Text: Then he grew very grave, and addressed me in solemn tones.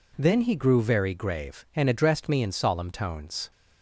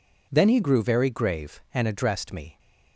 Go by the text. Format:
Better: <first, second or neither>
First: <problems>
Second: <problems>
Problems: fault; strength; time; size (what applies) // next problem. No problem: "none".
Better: first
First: none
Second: stops before "in solemn tones"; at 2.5 s